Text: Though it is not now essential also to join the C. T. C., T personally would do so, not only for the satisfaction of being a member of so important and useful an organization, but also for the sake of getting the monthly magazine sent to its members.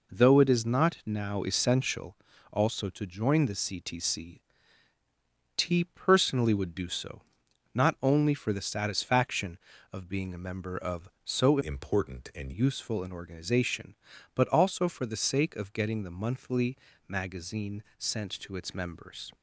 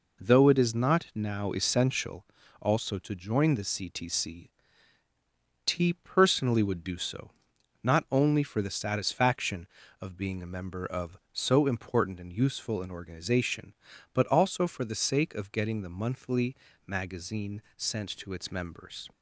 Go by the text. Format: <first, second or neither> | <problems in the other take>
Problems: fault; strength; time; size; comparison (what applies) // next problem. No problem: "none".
second | pauses between "essential" and "also"; slight; at 2.1 s; 0.36 s long; slight in the second // changes voice from "important" to "and"; from 11.6 to 12.5 s; 0.9 s long // pauses between "monthly" and "magazine"; slight; at 16.7 s; 0.32 s long; slight in the second // pauses between "magazine" and "sent"; slight; at 17.8 s; 0.16 s long; slight in the second